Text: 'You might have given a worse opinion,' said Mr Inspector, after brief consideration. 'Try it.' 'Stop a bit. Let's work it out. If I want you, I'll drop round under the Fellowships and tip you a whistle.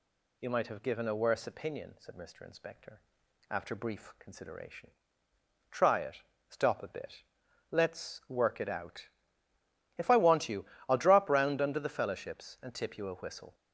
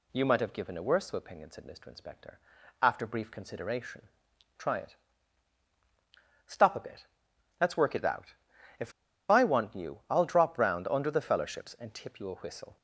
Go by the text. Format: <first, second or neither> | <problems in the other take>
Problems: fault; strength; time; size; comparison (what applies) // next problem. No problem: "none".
first | pauses between "If" and "I"; at 8.9 s; 0.38 s long